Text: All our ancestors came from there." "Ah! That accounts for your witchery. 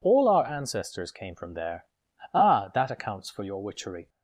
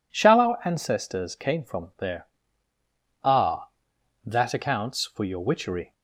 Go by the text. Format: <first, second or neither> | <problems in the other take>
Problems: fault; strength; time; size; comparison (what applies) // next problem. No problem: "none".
first | says "Shall" for "All"; at 0.1 s